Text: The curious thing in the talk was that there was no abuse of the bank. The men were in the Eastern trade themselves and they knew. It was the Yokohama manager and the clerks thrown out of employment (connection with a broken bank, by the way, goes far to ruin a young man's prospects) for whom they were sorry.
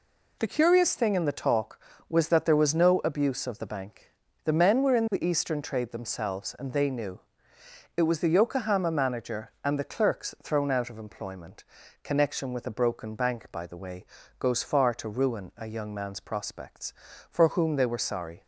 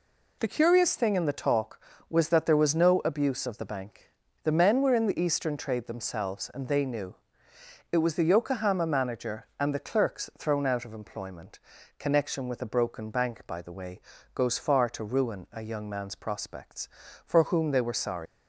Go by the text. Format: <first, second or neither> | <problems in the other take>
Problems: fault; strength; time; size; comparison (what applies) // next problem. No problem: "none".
first | leaves "sorry" unfinished; at 18.2 s; 120 ms